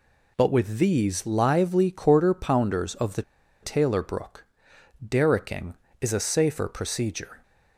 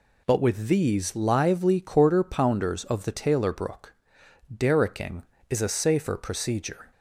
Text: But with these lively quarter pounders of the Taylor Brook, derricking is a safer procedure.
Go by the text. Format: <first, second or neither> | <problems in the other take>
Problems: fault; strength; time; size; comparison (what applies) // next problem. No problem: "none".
second | pauses between "the" and "Taylor"; at 3.2 s; 0.40 s long